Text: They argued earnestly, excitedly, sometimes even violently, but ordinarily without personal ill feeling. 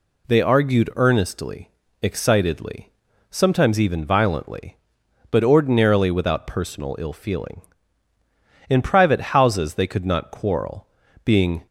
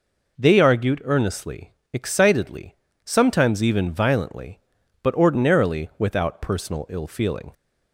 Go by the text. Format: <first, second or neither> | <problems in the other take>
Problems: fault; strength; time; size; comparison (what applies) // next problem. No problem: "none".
second | goes on to say "In private houses they could not quarrel being"; strong; from 8.6 s on; 2.9 s long